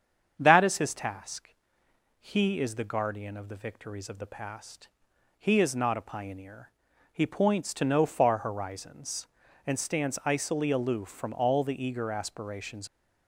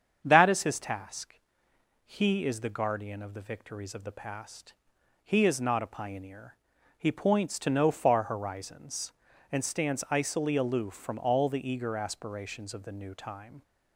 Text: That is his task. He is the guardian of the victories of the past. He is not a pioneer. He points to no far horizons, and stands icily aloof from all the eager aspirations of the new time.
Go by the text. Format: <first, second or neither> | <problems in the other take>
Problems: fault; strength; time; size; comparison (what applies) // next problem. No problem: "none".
second | starts louder than the rest; strong; until 1.3 s; 7.5 dB; strong in the second // stops before "of the new time"; at 12.8 s